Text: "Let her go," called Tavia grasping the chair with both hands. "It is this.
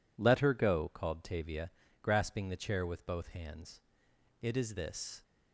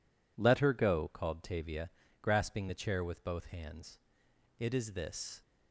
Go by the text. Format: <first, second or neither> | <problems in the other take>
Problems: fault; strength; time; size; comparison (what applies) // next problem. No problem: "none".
neither | pauses between "Tavia" and "grasping"; slight; the same in both